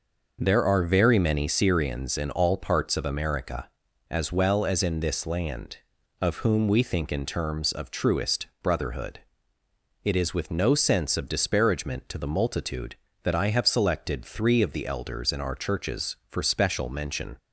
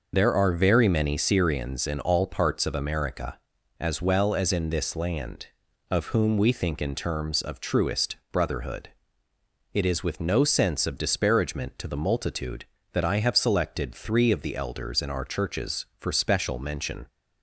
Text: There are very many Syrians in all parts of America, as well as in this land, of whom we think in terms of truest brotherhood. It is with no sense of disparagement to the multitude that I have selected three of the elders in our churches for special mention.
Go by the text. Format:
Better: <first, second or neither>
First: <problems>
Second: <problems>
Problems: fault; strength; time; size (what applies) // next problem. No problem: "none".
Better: first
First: pauses between "truest" and "brotherhood"; slight; at 8.4 s; 0.16 s long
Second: loses the start of "There"; at 0.1 s; 55 ms // pauses between "truest" and "brotherhood"; slight; at 8.1 s; 0.16 s long